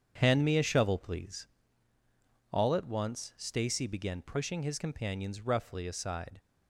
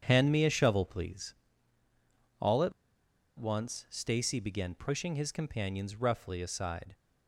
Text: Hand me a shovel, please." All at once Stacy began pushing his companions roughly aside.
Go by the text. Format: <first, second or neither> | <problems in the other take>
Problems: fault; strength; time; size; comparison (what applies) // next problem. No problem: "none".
first | starts louder than the rest; strong; until 1.0 s; 7.5 dB; strong in the first // pauses between "at" and "once"; noticeable; at 2.7 s; 0.67 s long